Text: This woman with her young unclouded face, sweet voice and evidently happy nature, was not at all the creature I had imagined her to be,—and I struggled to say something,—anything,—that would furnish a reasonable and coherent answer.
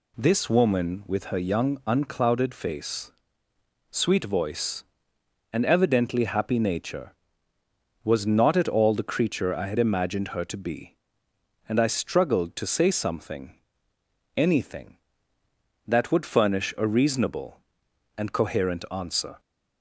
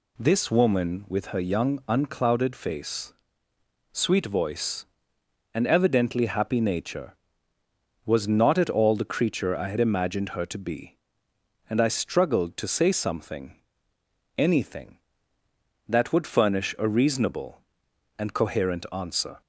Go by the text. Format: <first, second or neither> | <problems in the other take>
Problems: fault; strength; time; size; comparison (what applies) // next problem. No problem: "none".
neither | none